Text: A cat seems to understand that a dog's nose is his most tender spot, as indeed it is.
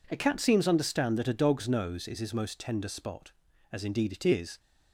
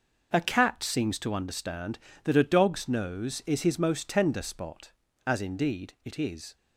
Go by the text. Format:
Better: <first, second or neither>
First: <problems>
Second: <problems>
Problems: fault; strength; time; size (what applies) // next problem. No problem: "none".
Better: second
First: skips "to"; at 0.6 s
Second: none